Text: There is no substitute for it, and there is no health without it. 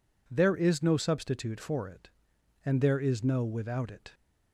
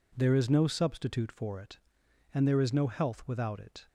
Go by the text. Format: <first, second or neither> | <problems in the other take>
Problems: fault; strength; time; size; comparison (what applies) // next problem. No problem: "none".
second | skips "health"; at 3.4 s